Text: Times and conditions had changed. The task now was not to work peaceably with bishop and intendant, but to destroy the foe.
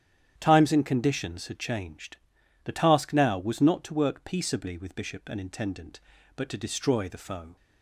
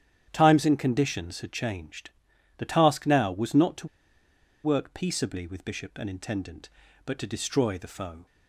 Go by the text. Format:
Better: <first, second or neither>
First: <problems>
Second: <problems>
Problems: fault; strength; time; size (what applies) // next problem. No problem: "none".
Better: first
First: starts louder than the rest; strong; until 1.4 s; 10 dB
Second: starts louder than the rest; strong; until 1.3 s; 10 dB // pauses between "to" and "work"; noticeable; at 3.8 s; 0.76 s long